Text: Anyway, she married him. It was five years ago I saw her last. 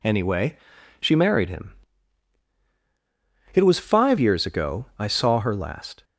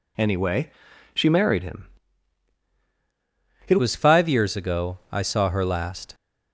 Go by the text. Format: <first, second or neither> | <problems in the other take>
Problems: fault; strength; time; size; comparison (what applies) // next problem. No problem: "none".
first | changes voice at "was"; from 3.7 s on; 2.4 s long // pauses between "ago" and "I"; slight; at 4.9 s; 0.16 s long